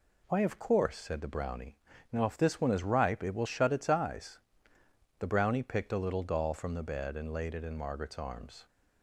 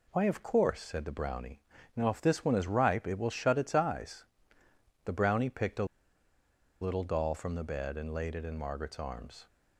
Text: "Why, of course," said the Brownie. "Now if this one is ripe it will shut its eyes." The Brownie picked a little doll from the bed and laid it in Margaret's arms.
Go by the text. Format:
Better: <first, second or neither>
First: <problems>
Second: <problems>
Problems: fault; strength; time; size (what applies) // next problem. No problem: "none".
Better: first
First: none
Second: pauses between "a" and "little"; noticeable; at 5.8 s; 0.96 s long